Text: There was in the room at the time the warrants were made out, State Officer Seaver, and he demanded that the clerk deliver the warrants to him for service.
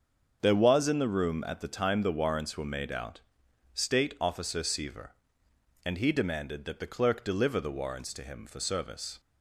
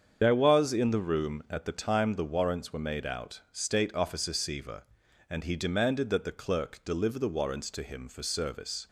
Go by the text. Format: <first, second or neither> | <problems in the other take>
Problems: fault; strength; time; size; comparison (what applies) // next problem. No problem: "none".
first | loses the start of "There"; at 0.2 s; 80 ms // starts louder than the rest; strong; until 1.2 s; 7.5 dB; also in the first